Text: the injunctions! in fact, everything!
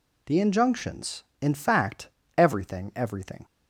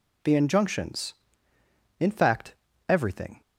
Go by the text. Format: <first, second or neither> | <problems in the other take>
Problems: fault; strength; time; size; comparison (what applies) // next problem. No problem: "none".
second | says "everything" twice; at 2.9 s